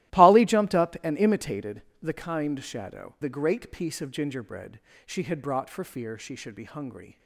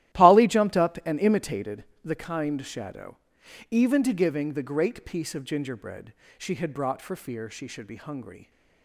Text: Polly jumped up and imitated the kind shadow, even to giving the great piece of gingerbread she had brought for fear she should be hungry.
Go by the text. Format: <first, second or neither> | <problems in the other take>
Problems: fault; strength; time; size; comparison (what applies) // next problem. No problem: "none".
second | starts louder than the rest; strong; until 1.2 s; 17 dB; strong in the second // pauses between "imitated" and "the"; slight; at 1.8 s; 0.20 s long; slight in the second // skips "even to giving"; at 3.1 s // pauses between "gingerbread" and "she"; slight; at 4.7 s; 0.26 s long; slight in the second